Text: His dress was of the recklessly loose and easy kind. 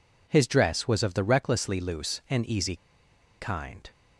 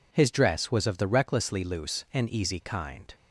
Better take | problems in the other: second | pauses between "easy" and "kind"; noticeable; at 2.7 s; 0.64 s long

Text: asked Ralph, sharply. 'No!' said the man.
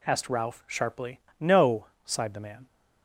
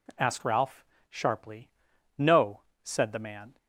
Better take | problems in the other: second | says "sighed" for "said"; at 2.0 s

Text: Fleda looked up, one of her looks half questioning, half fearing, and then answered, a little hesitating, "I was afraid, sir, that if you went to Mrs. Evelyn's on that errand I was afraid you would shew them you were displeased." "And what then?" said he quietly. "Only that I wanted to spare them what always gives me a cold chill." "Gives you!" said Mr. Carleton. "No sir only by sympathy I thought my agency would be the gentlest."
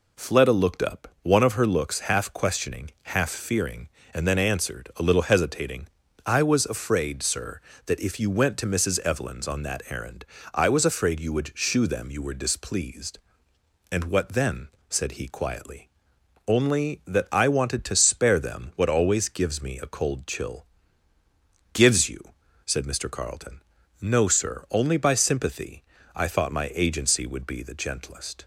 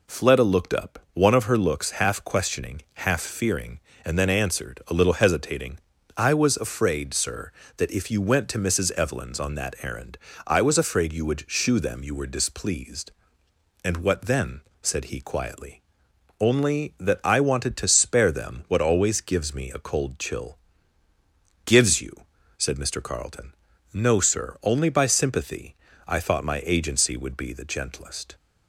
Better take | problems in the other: neither | pauses between "errand" and "I"; slight; the same in both // pauses between "sympathy" and "I"; slight; the same in both

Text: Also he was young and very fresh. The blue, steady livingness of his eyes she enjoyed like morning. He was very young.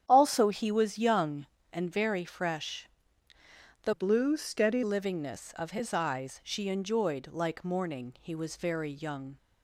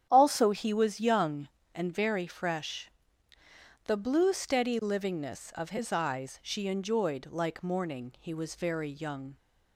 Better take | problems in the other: second | starts louder than the rest; strong; until 1.0 s; 9.5 dB; strong in the second // changes voice from "blue" to "steady"; from 3.9 to 4.8 s; 0.9 s long

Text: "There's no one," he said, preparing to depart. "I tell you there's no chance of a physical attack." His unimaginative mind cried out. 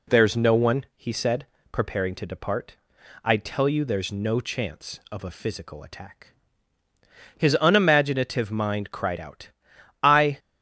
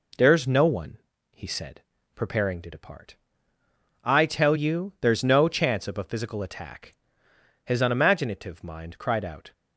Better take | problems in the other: second | goes on to say "I"; slight; from 10.0 s on; 0.34 s long

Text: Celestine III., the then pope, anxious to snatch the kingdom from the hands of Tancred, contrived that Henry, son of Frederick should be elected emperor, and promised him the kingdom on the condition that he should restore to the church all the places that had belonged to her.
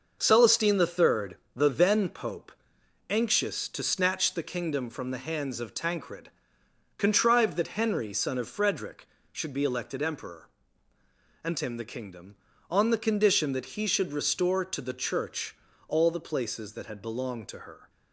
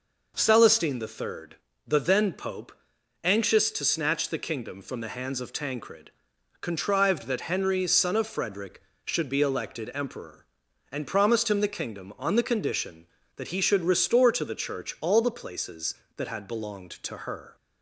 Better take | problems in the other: second | starts louder than the rest; noticeable; until 1.2 s; 6 dB // skips "promised"; at 11.5 s // pauses between "church" and "all"; slight; at 15.5 s; 0.32 s long

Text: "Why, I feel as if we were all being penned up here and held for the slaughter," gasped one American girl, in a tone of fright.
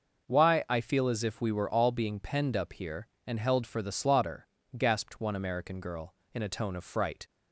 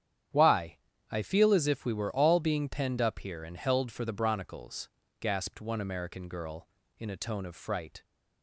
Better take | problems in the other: first | starts louder than the rest; strong; until 1.6 s; 9 dB // says "bronicles" for "slaughter"; at 4.1 s

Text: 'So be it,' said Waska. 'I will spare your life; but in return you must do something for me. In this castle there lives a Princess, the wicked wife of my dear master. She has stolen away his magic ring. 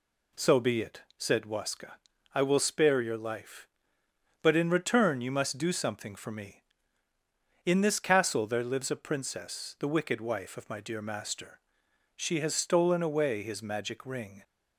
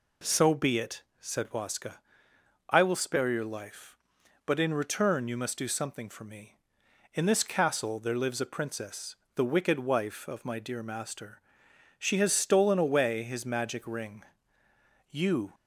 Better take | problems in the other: first | goes on to say "You"; slight; from 15.1 s on; 0.44 s long

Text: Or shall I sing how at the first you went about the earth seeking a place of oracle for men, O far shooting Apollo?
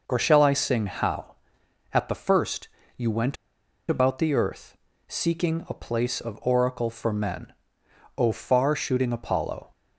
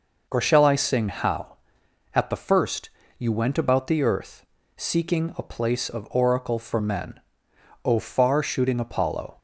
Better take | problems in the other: second | pauses between "first" and "you"; slight; at 2.6 s; 0.30 s long; slight in the second // pauses between "went" and "about"; noticeable; at 3.3 s; 0.53 s long // pauses between "earth" and "seeking"; slight; at 4.7 s; 0.32 s long; slight in the second

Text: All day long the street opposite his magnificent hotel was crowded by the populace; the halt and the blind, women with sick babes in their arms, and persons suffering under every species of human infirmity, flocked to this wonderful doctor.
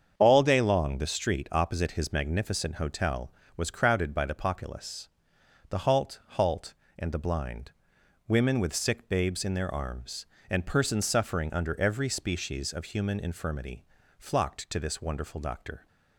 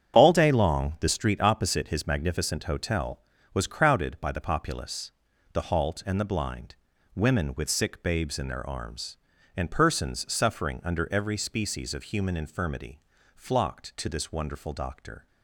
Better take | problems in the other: second | starts louder than the rest; strong; until 1.1 s; 7.5 dB; strong in the second // says "halt" twice; at 6.3 s

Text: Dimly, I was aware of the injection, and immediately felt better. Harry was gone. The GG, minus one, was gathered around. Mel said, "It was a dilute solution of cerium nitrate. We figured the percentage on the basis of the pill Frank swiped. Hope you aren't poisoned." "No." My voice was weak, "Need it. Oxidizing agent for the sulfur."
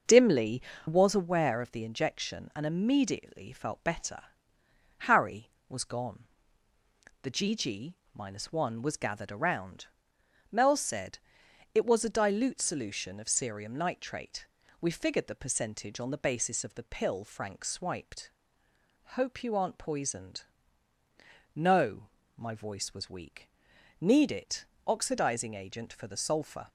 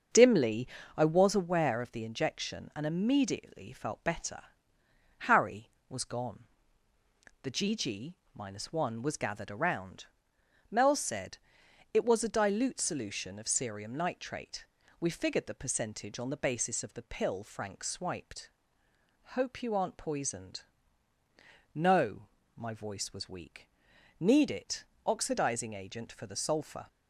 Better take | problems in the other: second | starts louder than the rest; until 1.3 s; 6.5 dB; also in the second // skips "I"; at 0.7 s

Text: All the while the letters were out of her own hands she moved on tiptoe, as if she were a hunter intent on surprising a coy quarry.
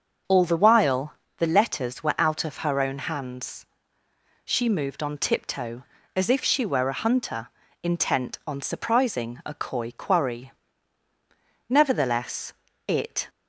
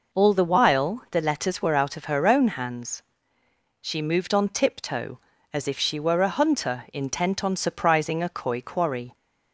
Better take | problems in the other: second | starts louder than the rest; until 1.5 s; 7 dB // pauses between "while" and "the"; slight; at 1.1 s; 0.24 s long // pauses between "hands" and "she"; noticeable; at 3.6 s; 0.80 s long; noticeable in the second // pauses between "hunter" and "intent"; slight; at 7.4 s; 0.34 s long // goes on to say "Nevertheless it"; from 11.6 s on; 1.5 s long

